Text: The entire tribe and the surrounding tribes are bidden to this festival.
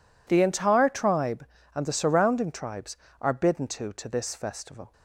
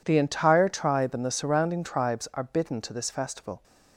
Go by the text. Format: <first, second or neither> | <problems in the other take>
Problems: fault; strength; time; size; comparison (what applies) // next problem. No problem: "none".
second | says "to" twice; at 3.9 s